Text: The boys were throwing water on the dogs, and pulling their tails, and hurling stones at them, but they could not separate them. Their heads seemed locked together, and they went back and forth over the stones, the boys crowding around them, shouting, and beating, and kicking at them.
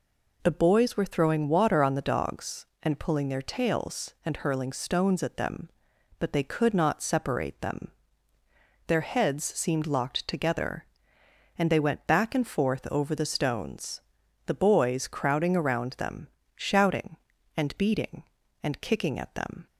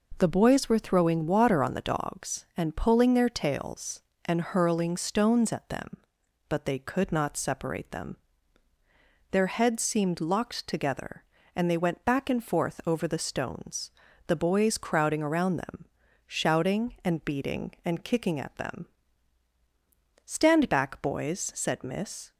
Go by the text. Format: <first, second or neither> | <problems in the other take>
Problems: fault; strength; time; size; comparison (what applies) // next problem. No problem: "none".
first | goes on to say "Stand back boys said Miss"; strong; from 20.2 s on; 2.0 s long